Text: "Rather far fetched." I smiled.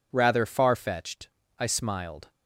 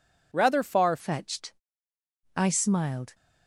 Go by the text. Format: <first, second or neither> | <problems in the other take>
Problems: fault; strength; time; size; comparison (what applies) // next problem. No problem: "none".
first | changes voice at "fetched"; from 0.9 s on; 2.2 s long